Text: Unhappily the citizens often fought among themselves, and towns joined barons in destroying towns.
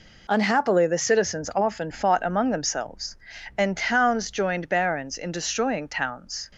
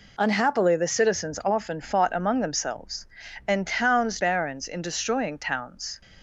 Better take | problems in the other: first | skips "joined"; at 4.1 s

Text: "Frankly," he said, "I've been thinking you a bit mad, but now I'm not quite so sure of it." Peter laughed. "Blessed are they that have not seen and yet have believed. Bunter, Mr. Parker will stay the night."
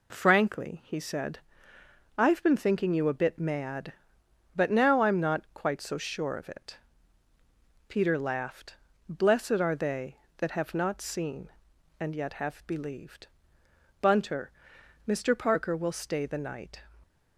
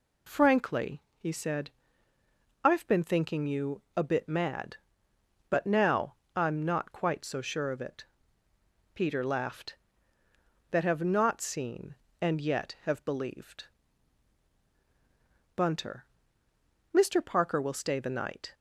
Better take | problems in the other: first | pauses between "now" and "I'm"; slight; at 6.1 s; 0.20 s long // skips "Blessed are they"; at 10.2 s

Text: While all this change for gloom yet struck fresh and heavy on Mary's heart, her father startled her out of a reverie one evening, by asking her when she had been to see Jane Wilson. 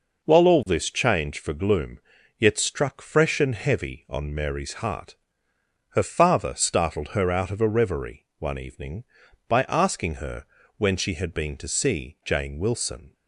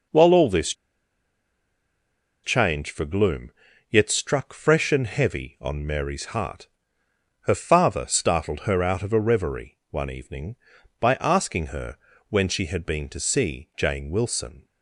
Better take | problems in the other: first | pauses between "this" and "change"; strong; at 0.7 s; 1.7 s long // pauses between "gloom" and "yet"; at 3.5 s; 0.40 s long; also in the first // pauses between "her" and "when"; slight; at 11.9 s; 0.34 s long; slight in the first

